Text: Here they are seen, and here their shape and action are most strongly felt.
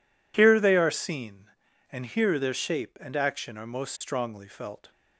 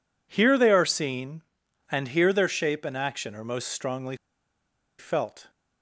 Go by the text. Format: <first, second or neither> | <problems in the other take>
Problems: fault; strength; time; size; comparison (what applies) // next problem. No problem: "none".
first | pauses between "strongly" and "felt"; noticeable; at 4.1 s; 0.84 s long